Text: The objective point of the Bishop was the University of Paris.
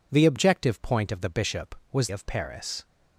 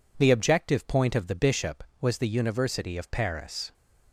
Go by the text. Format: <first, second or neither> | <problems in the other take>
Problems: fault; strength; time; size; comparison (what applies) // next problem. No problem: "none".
second | skips "the University"; at 2.0 s